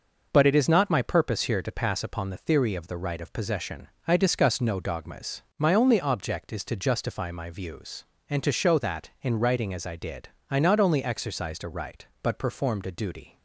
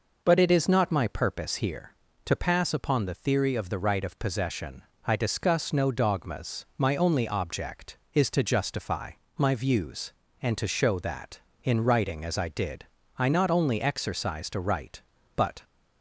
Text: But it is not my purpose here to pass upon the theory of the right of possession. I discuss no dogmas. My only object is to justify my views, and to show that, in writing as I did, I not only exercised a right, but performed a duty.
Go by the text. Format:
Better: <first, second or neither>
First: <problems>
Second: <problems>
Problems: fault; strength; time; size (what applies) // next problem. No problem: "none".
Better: first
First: none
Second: pauses between "justify" and "my"; slight; at 9.1 s; 0.24 s long // stops before "performed a duty"; at 15.6 s